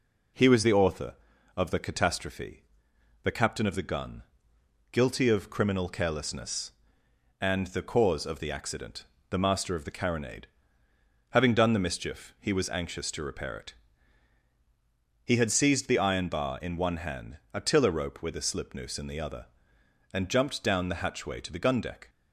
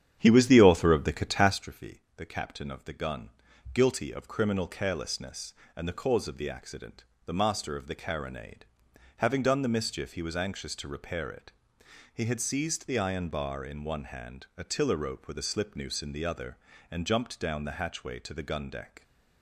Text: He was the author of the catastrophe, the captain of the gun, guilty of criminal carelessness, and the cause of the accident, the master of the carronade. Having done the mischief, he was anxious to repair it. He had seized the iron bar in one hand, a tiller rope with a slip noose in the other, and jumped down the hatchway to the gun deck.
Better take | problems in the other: first | starts louder than the rest; strong; until 1.6 s; 9.5 dB

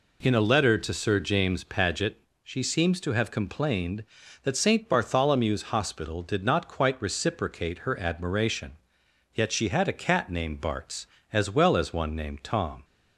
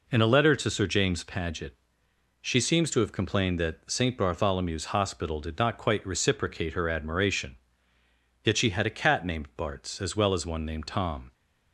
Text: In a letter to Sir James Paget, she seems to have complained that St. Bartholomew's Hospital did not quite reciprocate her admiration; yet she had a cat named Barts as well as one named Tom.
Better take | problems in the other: neither | none

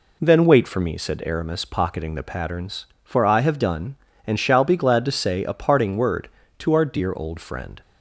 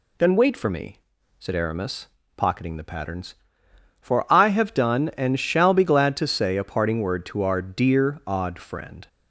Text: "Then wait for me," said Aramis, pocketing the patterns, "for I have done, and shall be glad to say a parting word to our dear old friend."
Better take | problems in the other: first | says "odd" for "old"; at 8.2 s

